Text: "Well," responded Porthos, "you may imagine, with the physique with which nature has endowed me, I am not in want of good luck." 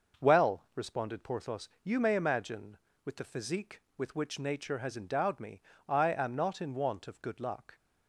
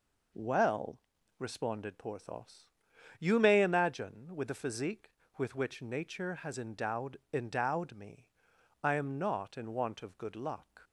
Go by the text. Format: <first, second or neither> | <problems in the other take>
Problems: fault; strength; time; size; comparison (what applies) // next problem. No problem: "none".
first | says "endowed" twice; at 7.3 s